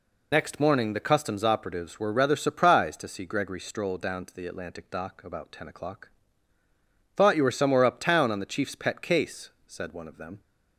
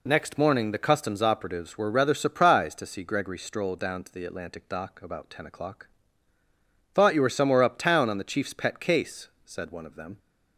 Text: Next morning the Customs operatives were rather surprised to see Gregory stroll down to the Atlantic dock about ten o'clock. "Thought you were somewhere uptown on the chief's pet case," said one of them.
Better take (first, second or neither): second